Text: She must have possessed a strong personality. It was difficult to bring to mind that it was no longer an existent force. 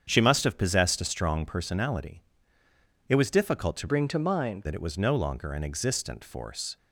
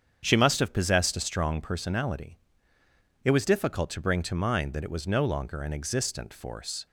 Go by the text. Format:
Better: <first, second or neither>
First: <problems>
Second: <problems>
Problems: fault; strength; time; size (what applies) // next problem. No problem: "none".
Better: second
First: starts louder than the rest; strong; until 1.0 s; 8 dB // changes voice from "bring" to "mind"; from 3.8 to 4.6 s; 0.8 s long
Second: starts louder than the rest; strong; until 1.2 s; 8 dB